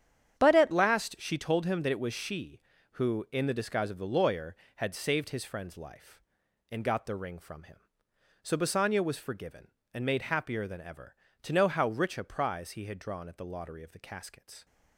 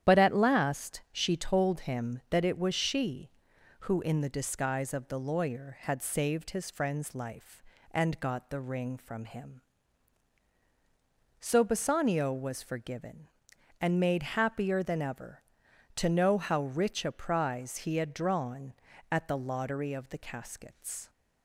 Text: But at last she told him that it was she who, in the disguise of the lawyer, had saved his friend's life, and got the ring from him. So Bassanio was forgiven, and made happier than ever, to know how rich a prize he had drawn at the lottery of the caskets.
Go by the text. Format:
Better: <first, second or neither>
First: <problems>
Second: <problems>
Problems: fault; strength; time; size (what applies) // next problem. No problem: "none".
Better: second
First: starts louder than the rest; strong; until 1.4 s; 9 dB // changes voice at "last"; from 0.7 s on; 13.9 s long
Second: starts louder than the rest; strong; until 1.1 s; 10 dB